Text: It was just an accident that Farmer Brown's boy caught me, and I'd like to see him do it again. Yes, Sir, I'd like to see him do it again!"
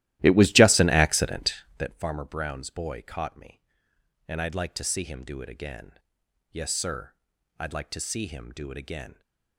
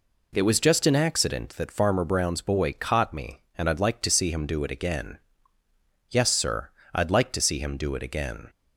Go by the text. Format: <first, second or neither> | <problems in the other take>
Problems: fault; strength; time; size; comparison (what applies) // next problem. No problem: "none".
second | starts louder than the rest; strong; until 2.0 s; 15 dB